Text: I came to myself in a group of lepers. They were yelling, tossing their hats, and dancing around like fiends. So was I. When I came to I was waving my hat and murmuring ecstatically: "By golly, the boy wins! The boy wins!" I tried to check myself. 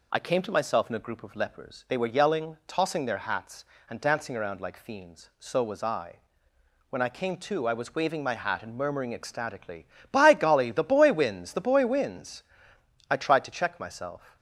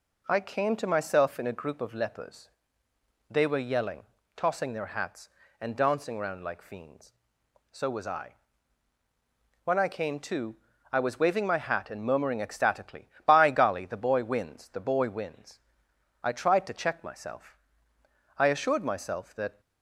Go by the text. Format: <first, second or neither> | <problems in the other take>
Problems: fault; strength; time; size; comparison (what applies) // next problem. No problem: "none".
first | pauses between "to" and "I"; slight; at 10.5 s; 0.34 s long // goes on to say "I assured myself that"; noticeable; from 18.3 s on; 1.2 s long